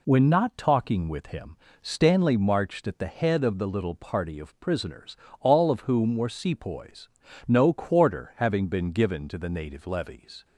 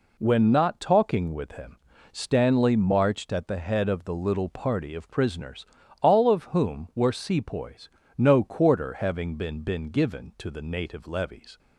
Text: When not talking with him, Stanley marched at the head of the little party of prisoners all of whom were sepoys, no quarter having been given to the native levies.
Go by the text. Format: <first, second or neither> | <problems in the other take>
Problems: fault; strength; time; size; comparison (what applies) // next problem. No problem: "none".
first | pauses between "prisoners" and "all"; at 5.6 s; 0.38 s long; slight in the first // says "been" twice; at 9.6 s